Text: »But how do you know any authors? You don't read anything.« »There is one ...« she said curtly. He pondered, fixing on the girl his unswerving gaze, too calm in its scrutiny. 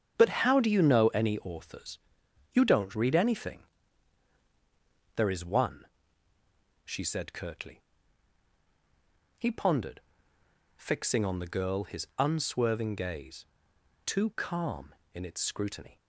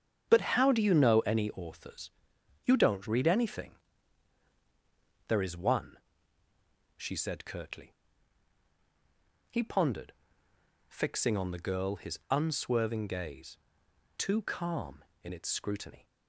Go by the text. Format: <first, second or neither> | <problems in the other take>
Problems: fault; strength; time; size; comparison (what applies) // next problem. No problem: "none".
neither | starts louder than the rest; strong; the same in both